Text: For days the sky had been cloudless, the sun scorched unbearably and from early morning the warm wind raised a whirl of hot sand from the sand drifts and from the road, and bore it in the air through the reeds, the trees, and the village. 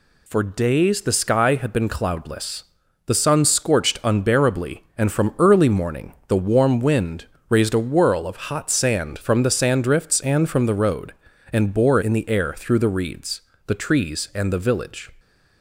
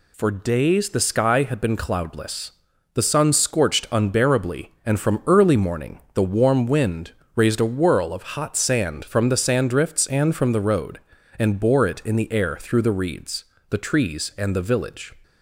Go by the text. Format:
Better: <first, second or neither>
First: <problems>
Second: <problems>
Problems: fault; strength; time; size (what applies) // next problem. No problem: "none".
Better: second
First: pauses between "wind" and "raised"; slight; at 7.2 s; 0.20 s long // skips "it"; at 12.0 s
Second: pauses between "wind" and "raised"; slight; at 7.1 s; 0.20 s long